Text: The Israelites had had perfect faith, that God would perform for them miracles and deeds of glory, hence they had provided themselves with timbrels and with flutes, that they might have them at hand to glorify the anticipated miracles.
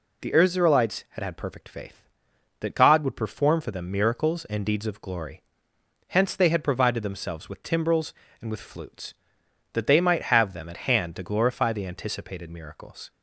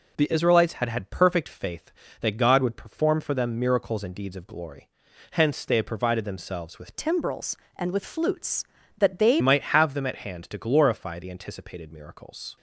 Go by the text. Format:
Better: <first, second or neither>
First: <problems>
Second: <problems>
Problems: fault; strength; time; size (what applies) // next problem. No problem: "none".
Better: first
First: none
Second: changes voice from "timbrels" to "they"; from 6.9 to 9.3 s; 2.4 s long